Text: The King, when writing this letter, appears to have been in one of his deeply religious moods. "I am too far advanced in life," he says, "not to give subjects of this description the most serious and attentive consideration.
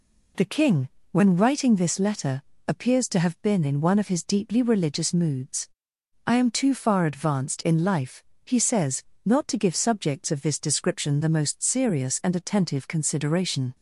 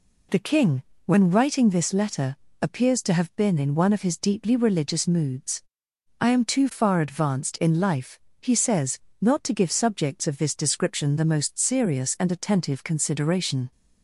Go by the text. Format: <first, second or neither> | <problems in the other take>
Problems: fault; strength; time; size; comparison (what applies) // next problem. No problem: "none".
neither | none